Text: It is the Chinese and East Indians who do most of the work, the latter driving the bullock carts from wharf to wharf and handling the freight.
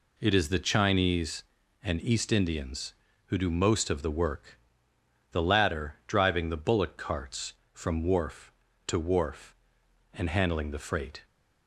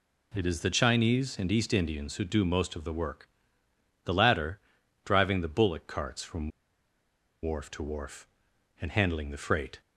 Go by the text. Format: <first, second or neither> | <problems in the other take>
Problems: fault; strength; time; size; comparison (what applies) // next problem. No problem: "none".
first | pauses between "latter" and "driving"; at 4.6 s; 0.44 s long // pauses between "from" and "wharf"; noticeable; at 6.4 s; 0.94 s long